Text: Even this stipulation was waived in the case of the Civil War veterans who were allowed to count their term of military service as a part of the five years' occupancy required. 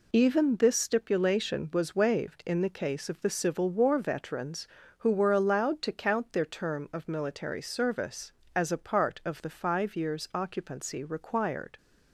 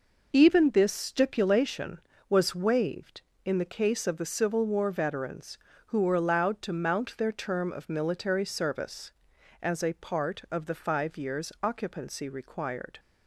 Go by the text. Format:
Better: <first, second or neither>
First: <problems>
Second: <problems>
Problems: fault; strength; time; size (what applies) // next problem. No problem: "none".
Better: first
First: none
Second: says "mount" for "count"; at 6.7 s